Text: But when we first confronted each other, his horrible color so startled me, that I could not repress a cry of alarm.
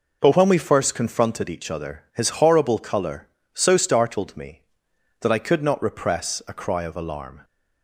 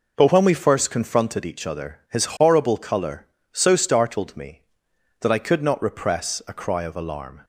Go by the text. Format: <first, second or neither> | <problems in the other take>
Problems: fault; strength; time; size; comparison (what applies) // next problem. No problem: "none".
neither | none